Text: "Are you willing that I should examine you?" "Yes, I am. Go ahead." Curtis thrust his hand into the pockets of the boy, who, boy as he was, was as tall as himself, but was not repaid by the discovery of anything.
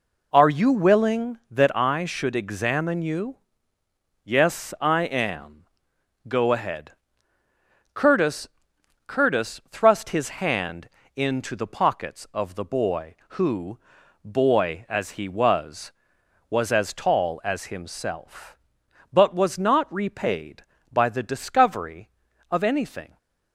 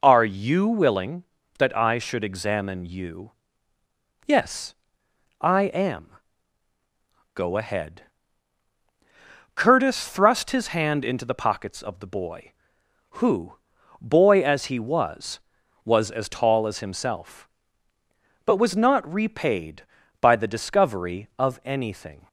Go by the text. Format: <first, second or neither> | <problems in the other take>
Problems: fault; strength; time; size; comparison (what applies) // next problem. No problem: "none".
second | says "Curtis" twice; at 9.0 s // pauses between "hand" and "into"; slight; at 10.8 s; 0.30 s long